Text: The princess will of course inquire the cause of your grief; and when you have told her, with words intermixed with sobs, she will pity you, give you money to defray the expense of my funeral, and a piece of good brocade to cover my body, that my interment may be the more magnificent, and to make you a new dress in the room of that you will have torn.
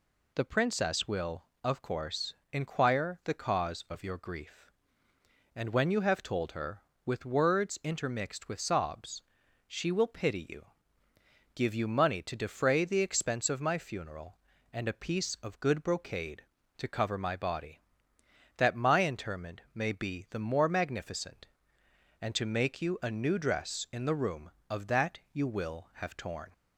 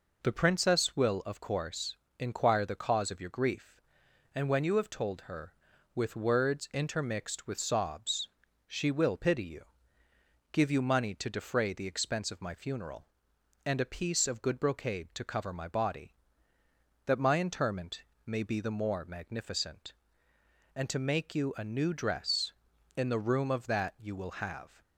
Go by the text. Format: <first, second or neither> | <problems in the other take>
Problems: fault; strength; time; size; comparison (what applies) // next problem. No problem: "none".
first | pauses between "course" and "inquire"; slight; at 1.9 s; 0.24 s long; slight in the first // pauses between "interment" and "may"; slight; at 18.0 s; 0.22 s long // stops before "torn"; at 24.8 s